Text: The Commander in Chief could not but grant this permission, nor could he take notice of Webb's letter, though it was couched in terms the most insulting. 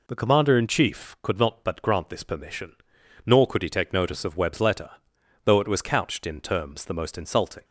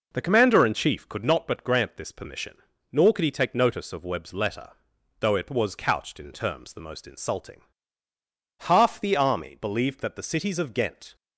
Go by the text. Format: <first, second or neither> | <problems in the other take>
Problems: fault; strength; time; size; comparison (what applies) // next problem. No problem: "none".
first | goes on to say "Half the army believed that the cities of Ghent"; strong; from 8.6 s on; 2.5 s long